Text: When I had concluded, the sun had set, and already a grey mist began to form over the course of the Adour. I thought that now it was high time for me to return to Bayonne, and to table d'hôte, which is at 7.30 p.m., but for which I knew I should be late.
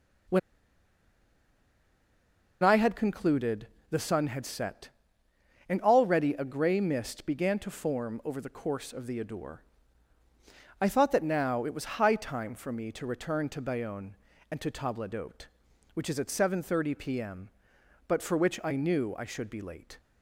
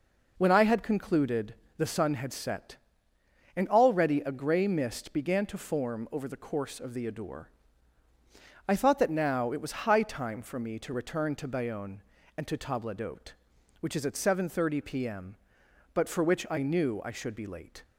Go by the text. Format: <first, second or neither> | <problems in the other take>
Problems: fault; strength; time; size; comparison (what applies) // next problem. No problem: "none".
second | pauses between "When" and "I"; strong; at 0.3 s; 2.2 s long